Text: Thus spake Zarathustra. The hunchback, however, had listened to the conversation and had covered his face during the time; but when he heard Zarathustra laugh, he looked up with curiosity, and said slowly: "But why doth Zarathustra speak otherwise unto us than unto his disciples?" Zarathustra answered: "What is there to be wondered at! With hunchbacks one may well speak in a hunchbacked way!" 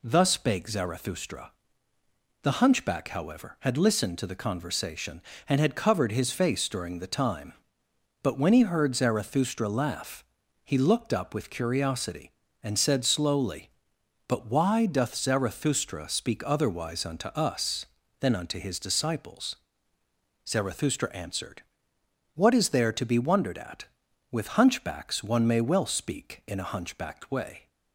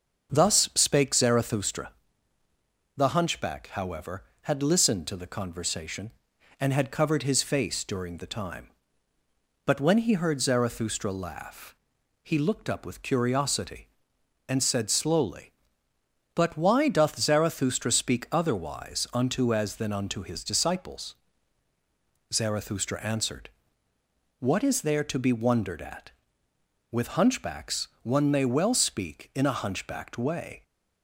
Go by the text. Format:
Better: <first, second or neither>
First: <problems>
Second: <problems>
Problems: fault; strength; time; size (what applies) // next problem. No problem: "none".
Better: first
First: none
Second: starts louder than the rest; until 1.3 s; 6.5 dB // says "as" for "us"; at 19.5 s // pauses between "hunchbacks" and "one"; slight; at 27.8 s; 0.16 s long